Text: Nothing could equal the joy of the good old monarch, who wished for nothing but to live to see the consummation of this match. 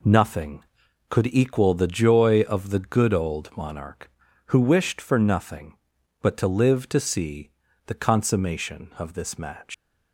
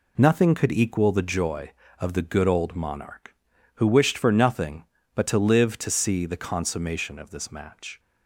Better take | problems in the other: second | pauses between "see" and "the"; at 7.4 s; 0.38 s long // leaves "match" unfinished; at 9.7 s; 150 ms

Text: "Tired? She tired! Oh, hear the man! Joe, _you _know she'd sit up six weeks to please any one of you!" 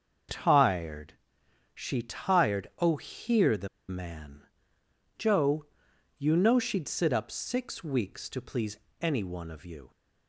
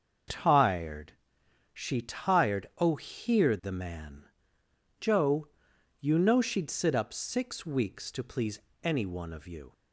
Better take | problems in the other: second | starts louder than the rest; until 1.9 s; 6.5 dB; also in the second // pauses between "the" and "man"; slight; at 3.6 s; 0.20 s long // pauses between "please" and "any"; slight; at 8.7 s; 0.24 s long; slight in the second

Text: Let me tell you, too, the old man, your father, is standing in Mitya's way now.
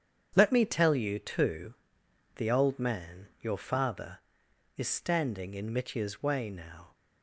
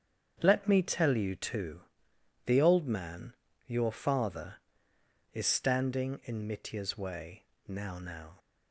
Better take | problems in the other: first | starts louder than the rest; strong; until 1.4 s; 7.5 dB; strong in the first // pauses between "way" and "now"; slight; at 7.4 s; 0.24 s long // says "now" twice; at 7.9 s

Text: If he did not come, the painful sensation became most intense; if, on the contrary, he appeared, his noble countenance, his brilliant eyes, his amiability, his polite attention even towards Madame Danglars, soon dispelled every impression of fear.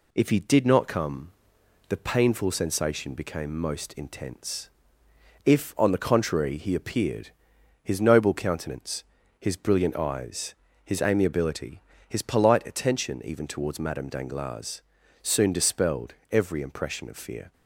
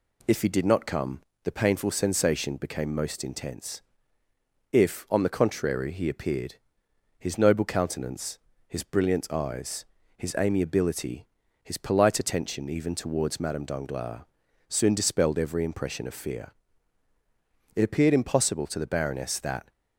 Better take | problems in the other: first | goes on to say "It appeared impossible to the baroness that"; strong; from 17.7 s on; 1.9 s long

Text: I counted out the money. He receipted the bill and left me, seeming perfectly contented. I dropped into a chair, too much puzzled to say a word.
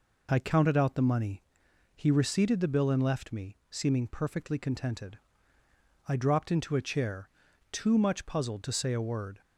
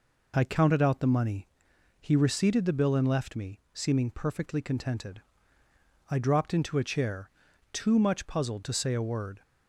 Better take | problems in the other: neither | none

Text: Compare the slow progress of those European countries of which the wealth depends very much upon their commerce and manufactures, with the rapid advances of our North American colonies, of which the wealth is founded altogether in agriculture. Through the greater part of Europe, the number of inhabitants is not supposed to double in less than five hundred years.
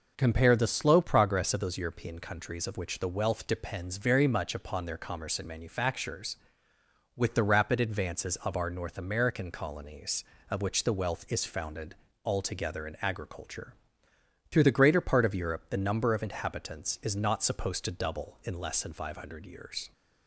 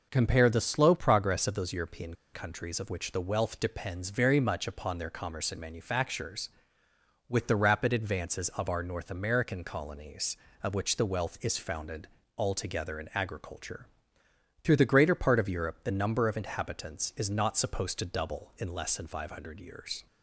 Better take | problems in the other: first | pauses between "European" and "countries"; slight; at 2.1 s; 0.18 s long // pauses between "founded" and "altogether"; slight; at 12.0 s; 0.28 s long; slight in the first

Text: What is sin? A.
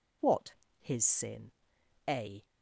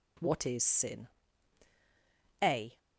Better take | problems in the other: second | says "his" for "is"; at 0.7 s

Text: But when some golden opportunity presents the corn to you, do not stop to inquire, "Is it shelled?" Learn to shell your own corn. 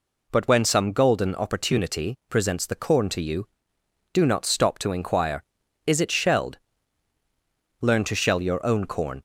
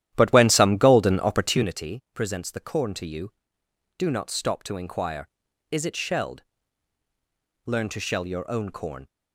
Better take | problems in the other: first | starts louder than the rest; strong; until 1.8 s; 12 dB

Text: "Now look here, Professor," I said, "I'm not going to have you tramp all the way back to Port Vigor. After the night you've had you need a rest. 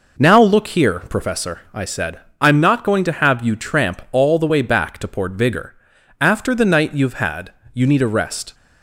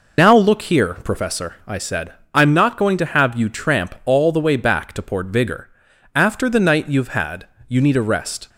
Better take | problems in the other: first | loses the start of "Now"; at 0.1 s; 70 ms // pauses between "had" and "you"; slight; at 7.4 s; 0.22 s long; slight in the first

